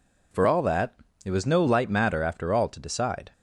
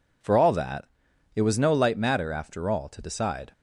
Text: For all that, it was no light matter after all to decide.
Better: neither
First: none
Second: none

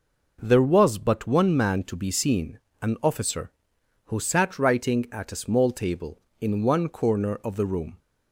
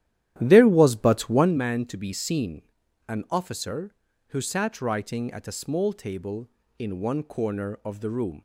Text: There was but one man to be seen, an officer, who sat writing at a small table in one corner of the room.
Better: first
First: none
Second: starts louder than the rest; strong; until 1.6 s; 12 dB

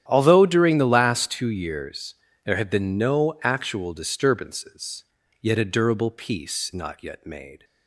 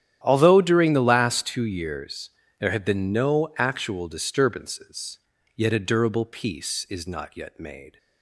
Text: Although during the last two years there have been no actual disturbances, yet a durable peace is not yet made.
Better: second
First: starts louder than the rest; strong; until 1.0 s; 10.5 dB // pauses between "years" and "there"; slight; at 2.1 s; 0.30 s long // skips "is"; at 6.7 s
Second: starts louder than the rest; strong; until 1.2 s; 11 dB // pauses between "years" and "there"; slight; at 2.3 s; 0.29 s long

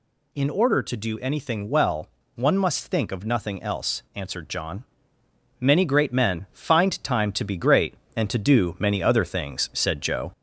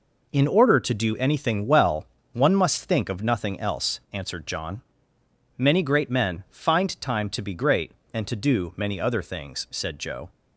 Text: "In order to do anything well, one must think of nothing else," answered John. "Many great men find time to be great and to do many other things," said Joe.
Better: second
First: gets louder; slight; throughout; 2.5 dB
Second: none

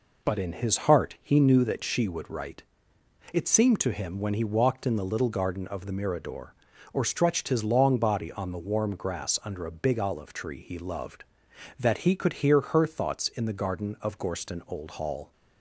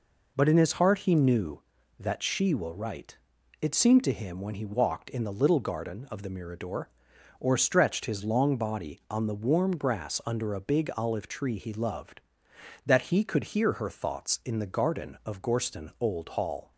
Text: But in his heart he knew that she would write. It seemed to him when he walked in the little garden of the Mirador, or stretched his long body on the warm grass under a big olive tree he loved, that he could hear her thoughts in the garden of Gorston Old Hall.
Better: first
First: none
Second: says "will" for "would"; at 2.5 s

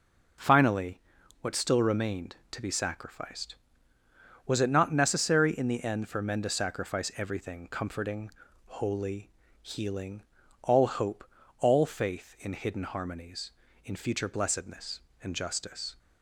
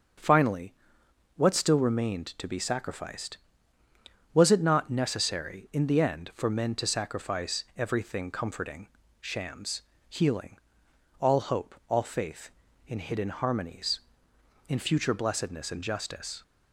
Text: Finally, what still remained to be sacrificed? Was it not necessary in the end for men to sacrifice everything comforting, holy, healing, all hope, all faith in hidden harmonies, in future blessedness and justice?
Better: first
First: none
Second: starts louder than the rest; until 1.8 s; 6.5 dB // says "shams" for "holy"; at 9.2 s

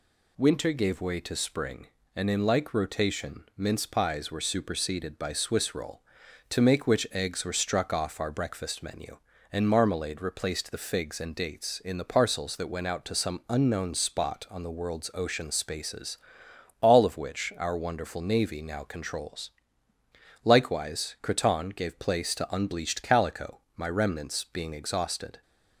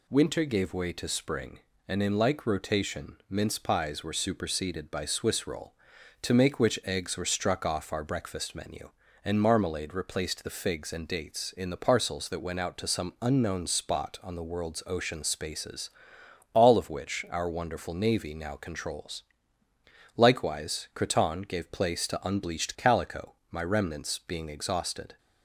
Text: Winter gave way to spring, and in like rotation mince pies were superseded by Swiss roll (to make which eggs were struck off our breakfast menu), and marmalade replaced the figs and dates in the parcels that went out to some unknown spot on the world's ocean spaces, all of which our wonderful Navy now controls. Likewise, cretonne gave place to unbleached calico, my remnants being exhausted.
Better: neither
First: none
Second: none

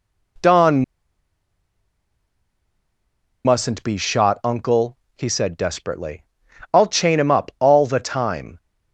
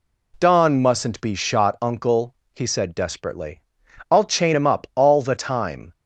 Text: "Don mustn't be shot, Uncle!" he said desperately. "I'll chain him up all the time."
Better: second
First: pauses between "Don" and "mustn't"; strong; at 0.8 s; 2.6 s long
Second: none

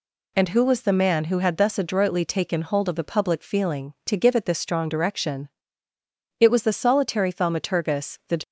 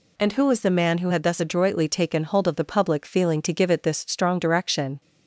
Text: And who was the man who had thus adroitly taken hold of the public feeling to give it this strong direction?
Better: second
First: goes on to say "It was the solitary Thaumaturgus the"; strong; from 6.3 s on; 2.0 s long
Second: none

